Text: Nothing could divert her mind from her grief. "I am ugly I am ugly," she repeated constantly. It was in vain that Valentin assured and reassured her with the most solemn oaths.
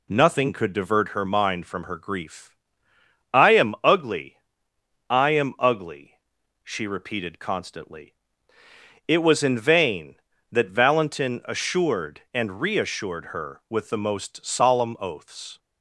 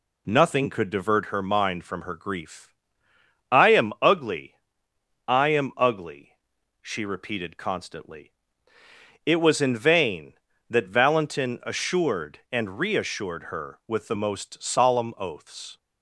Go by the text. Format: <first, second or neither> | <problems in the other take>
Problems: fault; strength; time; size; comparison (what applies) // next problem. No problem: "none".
neither | pauses between "ugly" and "I"; noticeable; the same in both